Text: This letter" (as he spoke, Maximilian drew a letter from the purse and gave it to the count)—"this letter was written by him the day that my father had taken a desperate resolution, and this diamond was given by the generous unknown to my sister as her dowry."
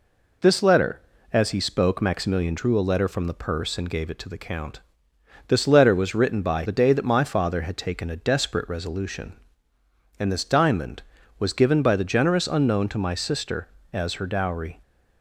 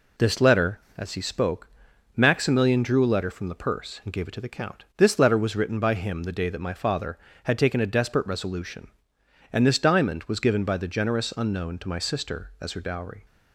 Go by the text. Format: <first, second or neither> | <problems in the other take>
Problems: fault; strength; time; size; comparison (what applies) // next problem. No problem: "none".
second | skips "him"; at 6.6 s